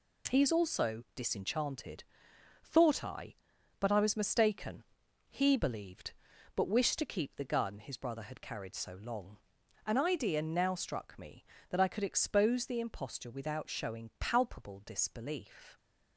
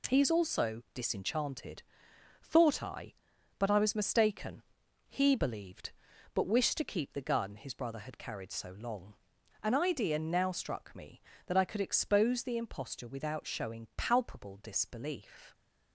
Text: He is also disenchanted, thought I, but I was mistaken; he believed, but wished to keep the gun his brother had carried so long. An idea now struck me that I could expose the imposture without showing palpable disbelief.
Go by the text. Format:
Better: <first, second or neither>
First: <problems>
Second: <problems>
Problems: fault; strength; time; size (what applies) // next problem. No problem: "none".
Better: neither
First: none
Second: none